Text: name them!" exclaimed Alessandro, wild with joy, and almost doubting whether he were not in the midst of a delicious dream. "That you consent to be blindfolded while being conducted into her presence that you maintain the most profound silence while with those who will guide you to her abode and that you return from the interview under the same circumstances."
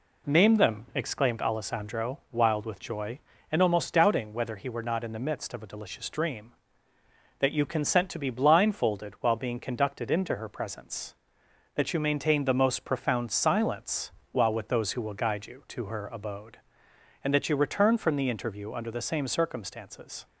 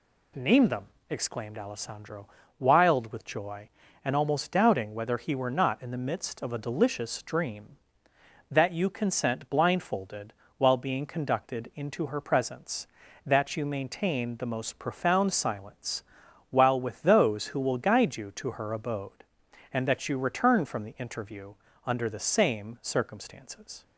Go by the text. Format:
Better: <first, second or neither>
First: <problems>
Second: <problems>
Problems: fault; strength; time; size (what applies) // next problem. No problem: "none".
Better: first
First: pauses between "silence" and "while"; slight; at 14.1 s; 0.20 s long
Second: skips "to be"; at 9.4 s // pauses between "blindfolded" and "while"; slight; at 10.3 s; 0.26 s long // pauses between "silence" and "while"; noticeable; at 16.0 s; 0.48 s long // pauses between "interview" and "under"; slight; at 21.5 s; 0.34 s long